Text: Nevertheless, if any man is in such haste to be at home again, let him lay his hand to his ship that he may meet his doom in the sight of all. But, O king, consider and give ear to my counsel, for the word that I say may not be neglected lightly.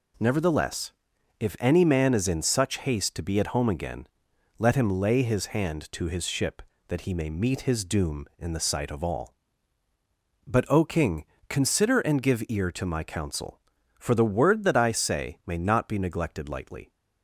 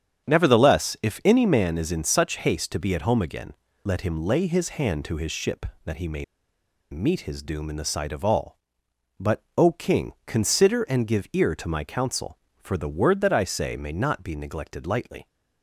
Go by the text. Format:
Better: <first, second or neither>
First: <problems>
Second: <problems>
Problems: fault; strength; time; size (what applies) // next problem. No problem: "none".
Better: first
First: none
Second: starts louder than the rest; strong; until 1.3 s; 8.5 dB // pauses between "may" and "meet"; noticeable; at 6.2 s; 0.67 s long